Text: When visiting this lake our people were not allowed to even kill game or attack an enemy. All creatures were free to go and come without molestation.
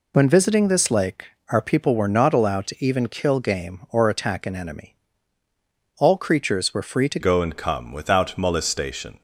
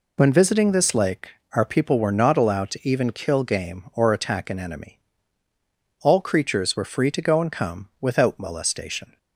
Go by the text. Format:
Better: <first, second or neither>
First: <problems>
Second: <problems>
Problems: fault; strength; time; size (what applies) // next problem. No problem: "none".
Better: second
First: pauses between "lake" and "our"; slight; at 1.2 s; 0.24 s long // changes voice at "go"; from 7.1 s on; 2.1 s long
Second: pauses between "lake" and "our"; slight; at 1.2 s; 0.24 s long